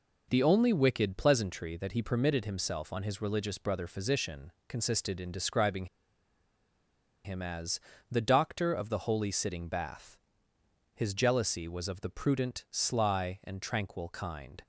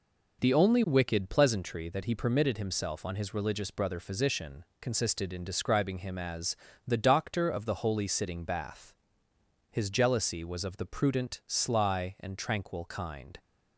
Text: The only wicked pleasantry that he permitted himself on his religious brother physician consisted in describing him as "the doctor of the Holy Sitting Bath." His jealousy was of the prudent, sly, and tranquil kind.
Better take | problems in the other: second | pauses between "physician" and "consisted"; slight; at 4.5 s; 0.16 s long; slight in the second // pauses between "describing" and "him"; strong; at 5.8 s; 1.3 s long // pauses between "as" and "the"; slight; at 7.7 s; 0.30 s long; slight in the second

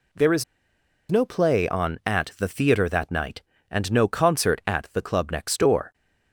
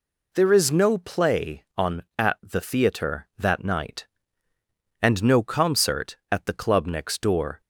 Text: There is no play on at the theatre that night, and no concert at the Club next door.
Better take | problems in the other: second | pauses between "is" and "no"; noticeable; at 0.4 s; 0.66 s long

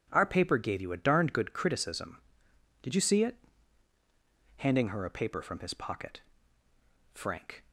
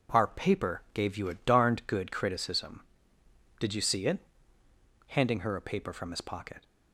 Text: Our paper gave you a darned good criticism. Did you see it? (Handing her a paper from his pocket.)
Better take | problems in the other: second | goes on to say "FRANK"; from 7.1 s on; 0.50 s long

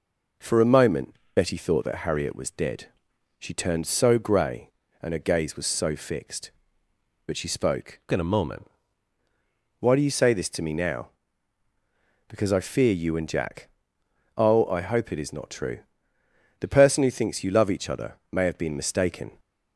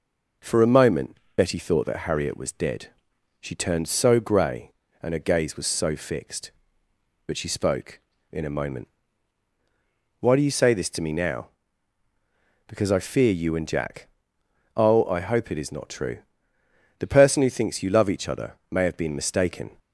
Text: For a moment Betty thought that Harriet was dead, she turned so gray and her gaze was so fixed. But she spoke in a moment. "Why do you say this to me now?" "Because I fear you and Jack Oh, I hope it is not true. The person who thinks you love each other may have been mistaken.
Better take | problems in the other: second | pauses between "moment" and "Betty"; slight; at 1.1 s; 0.20 s long; slight in the second // changes voice from "in" to "moment"; from 8.1 to 8.6 s; 0.5 s long // pauses between "Jack" and "Oh"; noticeable; at 13.6 s; 0.72 s long; noticeable in the second

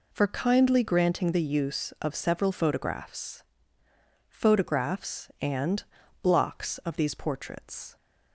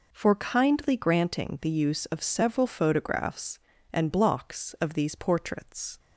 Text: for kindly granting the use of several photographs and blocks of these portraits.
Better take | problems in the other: second | says "photographs" twice; at 4.2 s // pauses between "and" and "blocks"; at 5.8 s; 0.38 s long

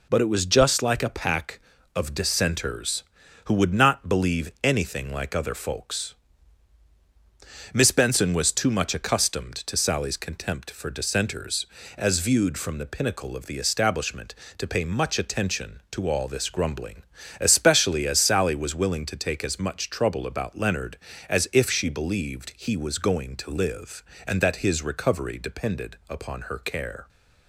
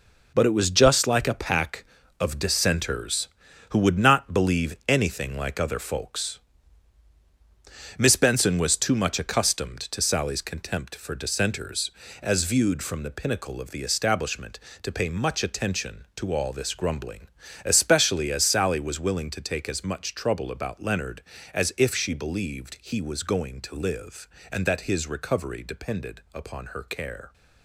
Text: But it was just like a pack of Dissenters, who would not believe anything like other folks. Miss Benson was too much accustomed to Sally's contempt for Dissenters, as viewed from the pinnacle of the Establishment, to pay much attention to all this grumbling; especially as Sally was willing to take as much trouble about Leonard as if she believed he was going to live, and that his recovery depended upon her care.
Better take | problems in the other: first | gets quieter; strong; throughout; 8.5 dB

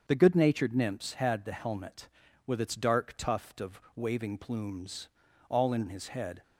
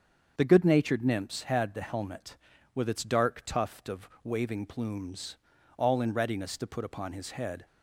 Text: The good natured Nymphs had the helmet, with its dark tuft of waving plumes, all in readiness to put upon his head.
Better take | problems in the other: second | starts louder than the rest; until 1.1 s; 6.5 dB; also in the second // pauses between "of" and "waving"; slight; at 3.7 s; 0.16 s long; slight in the second // skips "readiness to put upon"; at 5.8 s

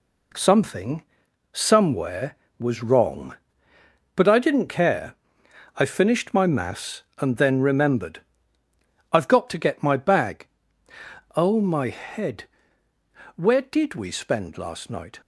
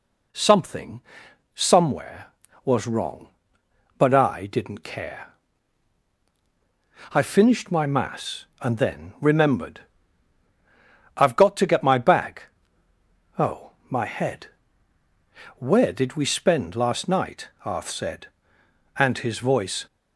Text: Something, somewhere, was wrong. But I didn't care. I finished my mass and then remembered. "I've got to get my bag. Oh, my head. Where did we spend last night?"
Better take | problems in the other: first | goes on to say "Arth said and his voice"; strong; from 17.6 s on; 2.2 s long

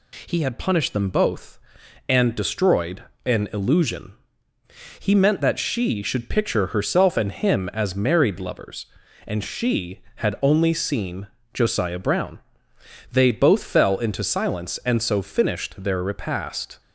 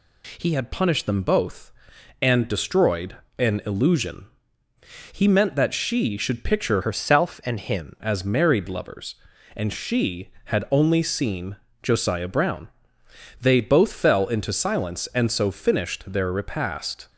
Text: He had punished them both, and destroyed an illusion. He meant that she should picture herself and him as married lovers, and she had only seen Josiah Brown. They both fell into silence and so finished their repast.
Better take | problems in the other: first | pauses between "destroyed" and "an"; slight; at 3.1 s; 0.20 s long; slight in the first // changes voice from "herself" to "him"; from 6.8 to 7.9 s; 1.1 s long // pauses between "seen" and "Josiah"; slight; at 11.5 s; 0.26 s long; slight in the first

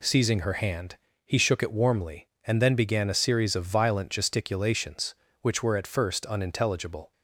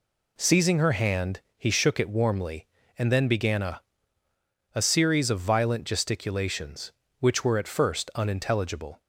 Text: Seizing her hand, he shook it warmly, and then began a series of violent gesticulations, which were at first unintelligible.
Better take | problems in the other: first | says "a" twice; at 4.7 s

